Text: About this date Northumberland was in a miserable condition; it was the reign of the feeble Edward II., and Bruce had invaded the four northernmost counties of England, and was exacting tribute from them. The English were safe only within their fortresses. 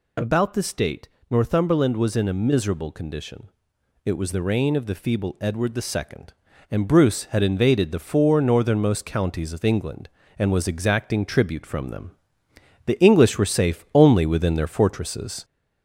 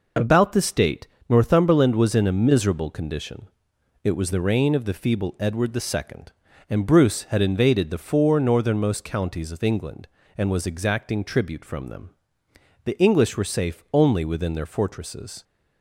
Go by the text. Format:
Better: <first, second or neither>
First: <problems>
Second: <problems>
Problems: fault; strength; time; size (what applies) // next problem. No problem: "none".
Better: second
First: gets louder; slight; throughout; 2 dB // pauses between "date" and "Northumberland"; slight; at 1.0 s; 0.24 s long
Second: pauses between "date" and "Northumberland"; slight; at 1.0 s; 0.24 s long